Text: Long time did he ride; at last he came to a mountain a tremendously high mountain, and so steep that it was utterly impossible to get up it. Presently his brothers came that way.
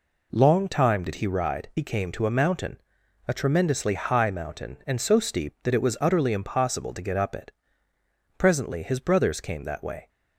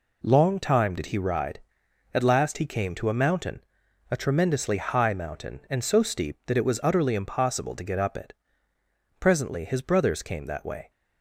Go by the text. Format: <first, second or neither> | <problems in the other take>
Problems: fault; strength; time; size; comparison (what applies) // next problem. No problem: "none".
second | skips "at last"; at 1.7 s // pauses between "mountain" and "a"; noticeable; at 2.8 s; 0.48 s long; noticeable in the second